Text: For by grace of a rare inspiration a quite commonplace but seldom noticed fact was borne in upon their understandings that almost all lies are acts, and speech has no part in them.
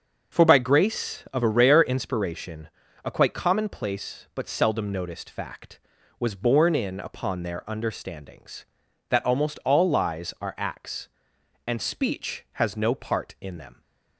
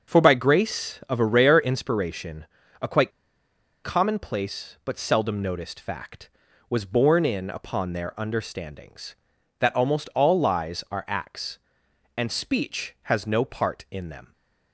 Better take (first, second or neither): first